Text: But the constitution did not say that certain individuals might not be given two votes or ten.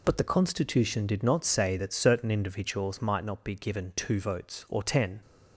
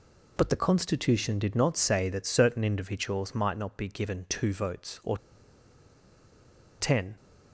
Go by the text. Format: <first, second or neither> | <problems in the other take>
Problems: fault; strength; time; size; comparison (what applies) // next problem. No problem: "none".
first | pauses between "or" and "ten"; strong; at 5.1 s; 1.6 s long